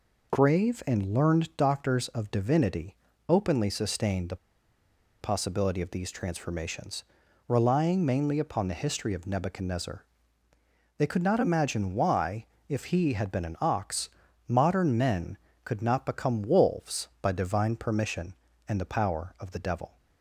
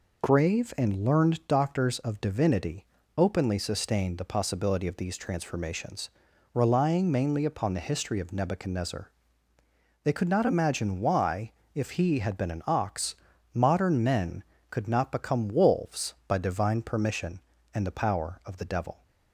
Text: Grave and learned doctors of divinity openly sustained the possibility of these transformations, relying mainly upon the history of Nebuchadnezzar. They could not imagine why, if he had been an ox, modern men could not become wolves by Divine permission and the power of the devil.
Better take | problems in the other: second | pauses between "divinity" and "openly"; slight; at 2.9 s; 0.32 s long; slight in the second // pauses between "the" and "possibility"; noticeable; at 4.3 s; 0.85 s long

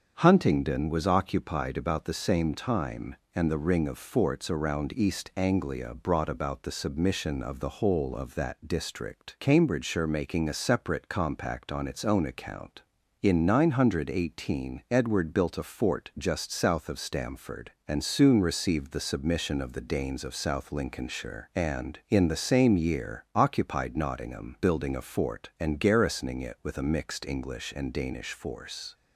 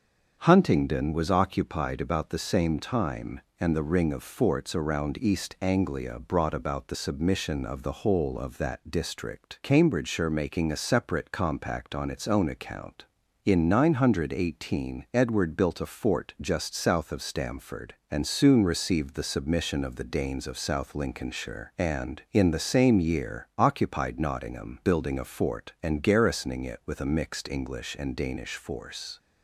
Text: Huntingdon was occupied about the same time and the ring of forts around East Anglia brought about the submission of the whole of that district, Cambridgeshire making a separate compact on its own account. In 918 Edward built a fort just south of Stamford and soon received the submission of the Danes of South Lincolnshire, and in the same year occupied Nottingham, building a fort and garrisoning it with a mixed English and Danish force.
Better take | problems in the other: neither | starts louder than the rest; the same in both

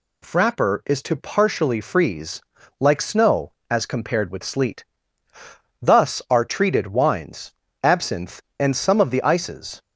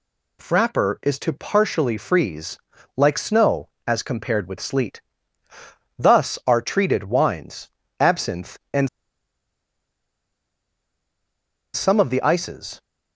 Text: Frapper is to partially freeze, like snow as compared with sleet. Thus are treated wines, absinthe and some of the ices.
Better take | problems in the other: first | pauses between "and" and "some"; strong; at 8.8 s; 2.8 s long

